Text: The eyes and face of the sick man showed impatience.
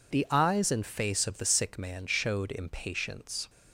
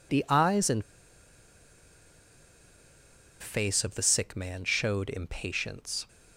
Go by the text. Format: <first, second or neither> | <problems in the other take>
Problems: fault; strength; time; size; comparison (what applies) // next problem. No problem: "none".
first | pauses between "and" and "face"; strong; at 0.8 s; 2.5 s long